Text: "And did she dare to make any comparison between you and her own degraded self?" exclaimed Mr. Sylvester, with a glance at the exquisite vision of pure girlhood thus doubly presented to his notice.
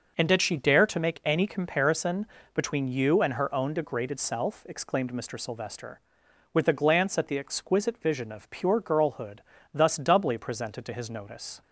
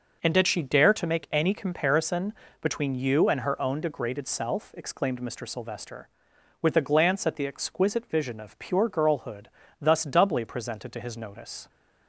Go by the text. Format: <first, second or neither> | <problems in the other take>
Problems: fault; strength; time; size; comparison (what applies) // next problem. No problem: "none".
neither | pauses between "comparison" and "between"; slight; the same in both // pauses between "girlhood" and "thus"; slight; the same in both